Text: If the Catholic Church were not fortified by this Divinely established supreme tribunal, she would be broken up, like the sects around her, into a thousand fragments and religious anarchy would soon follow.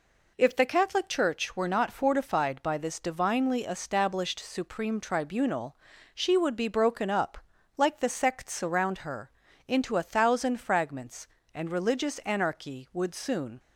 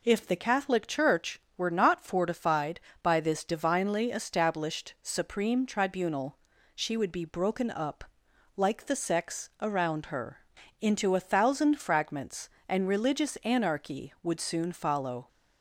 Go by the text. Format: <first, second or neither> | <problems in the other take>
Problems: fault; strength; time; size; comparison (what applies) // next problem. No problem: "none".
second | stops before "follow"; at 13.5 s